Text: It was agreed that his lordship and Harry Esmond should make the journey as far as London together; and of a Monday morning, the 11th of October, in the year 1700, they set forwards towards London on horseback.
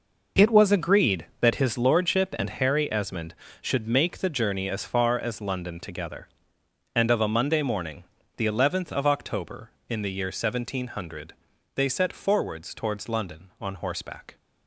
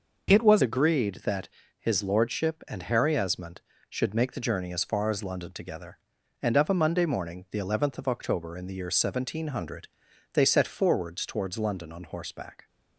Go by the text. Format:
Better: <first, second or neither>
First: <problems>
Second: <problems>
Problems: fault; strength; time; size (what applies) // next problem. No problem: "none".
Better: first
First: none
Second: changes voice at "agreed"; from 0.6 s on; 12.0 s long // pauses between "that" and "his"; slight; at 1.4 s; 0.30 s long